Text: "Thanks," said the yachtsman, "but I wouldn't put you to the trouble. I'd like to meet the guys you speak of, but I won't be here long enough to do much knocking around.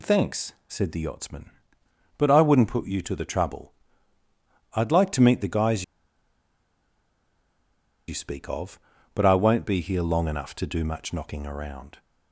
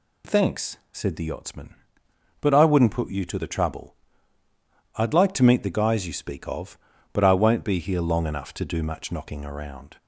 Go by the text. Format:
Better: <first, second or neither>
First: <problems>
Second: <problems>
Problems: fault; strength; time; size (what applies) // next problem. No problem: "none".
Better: second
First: pauses between "guys" and "you"; strong; at 5.8 s; 2.2 s long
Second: none